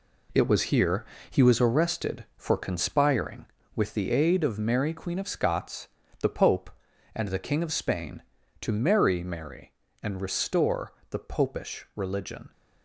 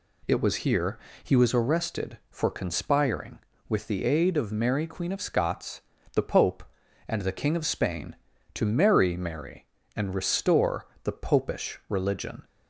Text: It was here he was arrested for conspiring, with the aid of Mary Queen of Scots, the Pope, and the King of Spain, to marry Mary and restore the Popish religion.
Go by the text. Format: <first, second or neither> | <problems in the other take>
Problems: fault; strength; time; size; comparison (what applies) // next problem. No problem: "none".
second | gets quieter; throughout; 7 dB // pauses between "here" and "he"; slight; at 1.0 s; 0.24 s long; slight in the second // pauses between "restore" and "the"; slight; at 10.9 s; 0.18 s long; slight in the second